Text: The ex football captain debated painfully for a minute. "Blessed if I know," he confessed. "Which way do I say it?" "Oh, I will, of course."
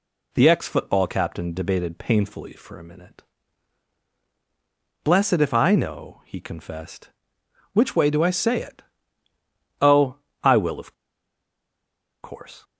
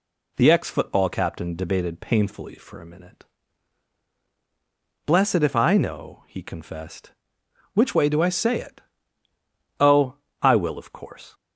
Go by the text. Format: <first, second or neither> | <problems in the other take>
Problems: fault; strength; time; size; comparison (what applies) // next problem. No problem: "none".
second | pauses between "of" and "course"; strong; at 10.9 s; 1.2 s long